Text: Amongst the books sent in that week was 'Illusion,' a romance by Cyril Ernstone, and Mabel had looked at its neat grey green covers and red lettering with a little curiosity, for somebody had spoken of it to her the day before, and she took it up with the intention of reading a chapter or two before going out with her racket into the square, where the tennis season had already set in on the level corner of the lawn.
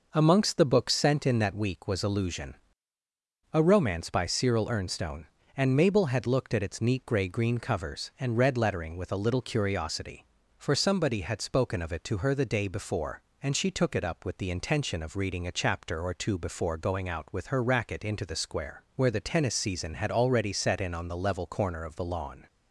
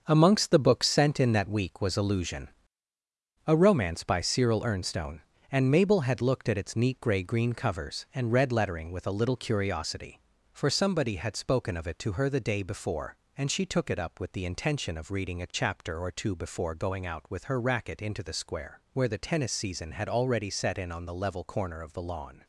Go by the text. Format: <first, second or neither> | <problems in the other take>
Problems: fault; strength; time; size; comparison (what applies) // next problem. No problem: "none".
first | gets quieter; strong; throughout; 8 dB